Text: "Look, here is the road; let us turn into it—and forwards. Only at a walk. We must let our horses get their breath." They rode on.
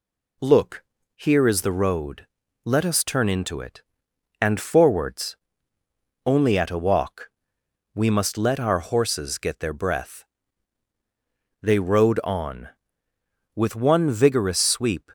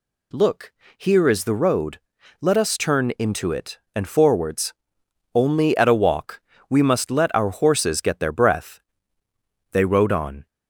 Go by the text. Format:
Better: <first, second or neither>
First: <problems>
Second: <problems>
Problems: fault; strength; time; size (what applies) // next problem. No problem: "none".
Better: second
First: goes on to say "With one vigorous sweep"; from 13.5 s on; 1.5 s long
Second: none